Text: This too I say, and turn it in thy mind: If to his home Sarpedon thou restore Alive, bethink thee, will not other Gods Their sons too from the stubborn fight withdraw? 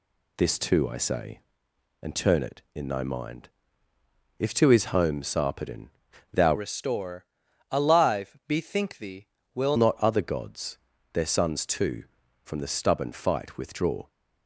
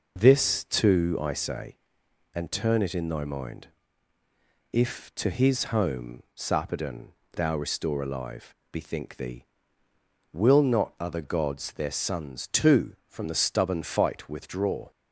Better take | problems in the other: second | pauses between "Sarpedon" and "thou"; noticeable; at 5.8 s; 0.46 s long; slight in the second // changes voice from "restore" to "will"; from 6.5 to 9.7 s; 3.2 s long // pauses between "restore" and "Alive"; noticeable; at 7.2 s; 0.46 s long // pauses between "Gods" and "Their"; slight; at 10.7 s; 0.34 s long

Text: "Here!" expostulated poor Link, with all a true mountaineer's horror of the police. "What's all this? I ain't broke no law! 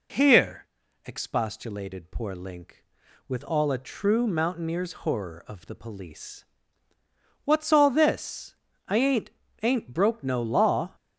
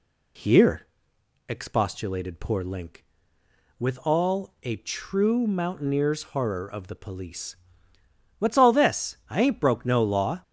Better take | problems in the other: second | says "ain't" twice; at 9.6 s

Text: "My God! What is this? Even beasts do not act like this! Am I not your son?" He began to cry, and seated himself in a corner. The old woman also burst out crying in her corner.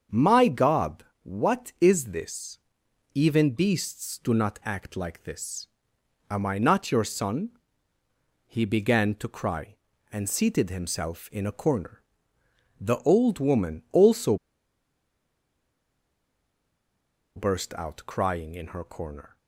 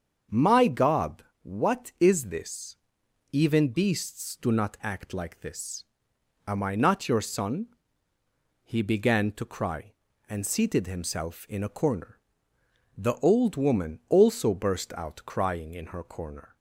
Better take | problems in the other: second | starts louder than the rest; strong; until 1.2 s; 7 dB; strong in the second // pauses between "also" and "burst"; strong; at 14.3 s; 3.0 s long

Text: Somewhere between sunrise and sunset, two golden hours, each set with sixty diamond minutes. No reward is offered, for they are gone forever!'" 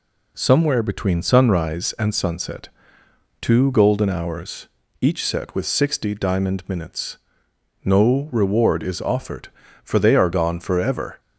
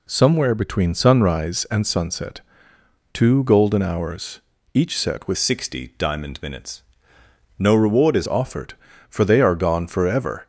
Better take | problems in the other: first | changes voice from "sixty" to "is"; from 5.3 to 8.2 s; 2.9 s long

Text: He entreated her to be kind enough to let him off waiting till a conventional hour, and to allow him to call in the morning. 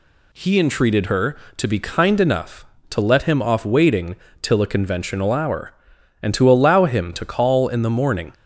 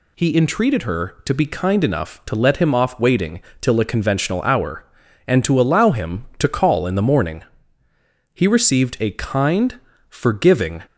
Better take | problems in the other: first | pauses between "waiting" and "till"; slight; at 3.4 s; 0.18 s long; slight in the first // goes on to say "He received a kind forgiving"; strong; from 8.3 s on; 2.5 s long

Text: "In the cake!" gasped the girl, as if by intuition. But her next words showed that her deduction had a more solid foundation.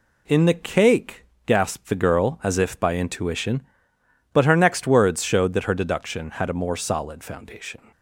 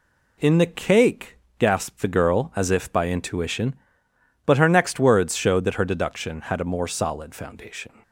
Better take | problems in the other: neither | none

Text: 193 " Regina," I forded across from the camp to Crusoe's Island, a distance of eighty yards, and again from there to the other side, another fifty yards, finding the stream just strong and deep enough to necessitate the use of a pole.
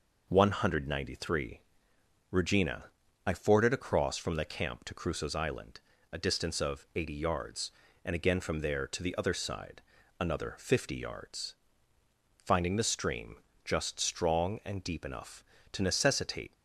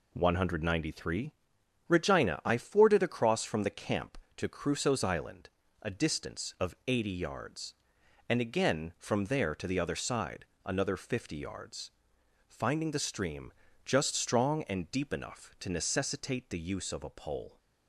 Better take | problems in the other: second | pauses between "stream" and "just"; slight; at 13.3 s; 0.28 s long; slight in the second // stops before "the use of a pole"; at 16.5 s

